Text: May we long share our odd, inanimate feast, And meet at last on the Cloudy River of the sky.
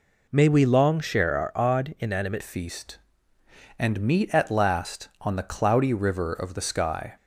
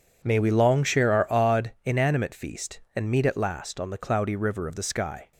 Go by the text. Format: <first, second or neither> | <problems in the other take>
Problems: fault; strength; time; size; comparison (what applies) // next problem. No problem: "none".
second | changes voice at "feast"; from 2.4 s on; 4.7 s long